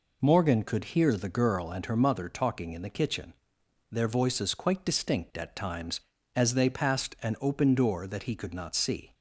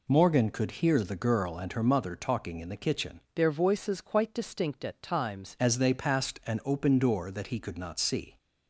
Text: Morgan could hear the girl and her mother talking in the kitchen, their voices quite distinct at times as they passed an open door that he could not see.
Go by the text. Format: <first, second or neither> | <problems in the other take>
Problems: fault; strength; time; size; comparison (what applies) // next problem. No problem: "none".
first | changes voice from "their" to "times"; from 3.3 to 5.5 s; 2.2 s long